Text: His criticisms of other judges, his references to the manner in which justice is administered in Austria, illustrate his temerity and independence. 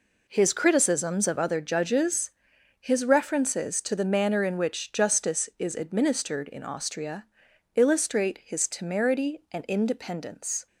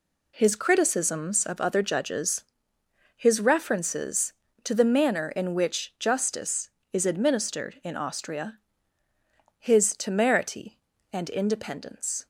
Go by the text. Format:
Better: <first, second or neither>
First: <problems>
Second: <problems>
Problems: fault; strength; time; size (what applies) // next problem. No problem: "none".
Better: first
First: none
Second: skips "illustrate"; at 9.0 s